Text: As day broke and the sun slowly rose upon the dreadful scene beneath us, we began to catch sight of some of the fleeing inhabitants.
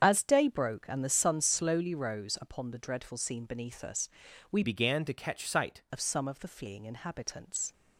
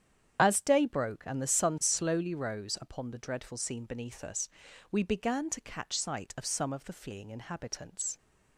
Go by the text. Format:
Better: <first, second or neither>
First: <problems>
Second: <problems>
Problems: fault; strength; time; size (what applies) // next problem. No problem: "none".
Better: second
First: starts louder than the rest; until 1.0 s; 7 dB // changes voice from "began" to "sight"; from 4.6 to 5.8 s; 1.2 s long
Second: starts louder than the rest; strong; until 1.4 s; 8 dB